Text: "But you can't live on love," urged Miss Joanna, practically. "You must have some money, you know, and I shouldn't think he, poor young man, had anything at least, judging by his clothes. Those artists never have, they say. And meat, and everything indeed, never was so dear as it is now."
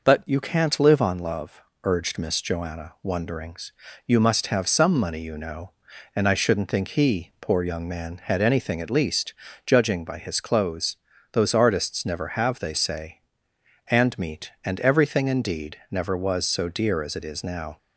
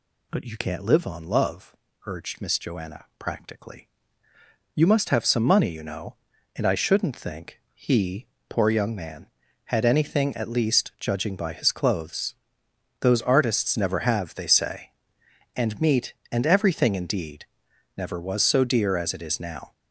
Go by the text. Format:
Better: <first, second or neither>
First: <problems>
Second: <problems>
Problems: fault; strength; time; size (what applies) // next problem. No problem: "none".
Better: second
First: says "wonderings" for "practically"; at 3.0 s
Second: none